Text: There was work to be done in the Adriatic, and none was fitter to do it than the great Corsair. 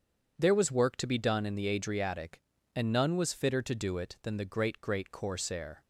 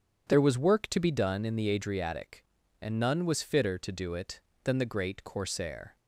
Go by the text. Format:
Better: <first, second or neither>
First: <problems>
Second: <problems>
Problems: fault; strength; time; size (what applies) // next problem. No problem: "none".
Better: second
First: starts louder than the rest; strong; until 1.3 s; 7.5 dB // says "great" twice; at 4.8 s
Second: starts louder than the rest; strong; until 1.3 s; 8 dB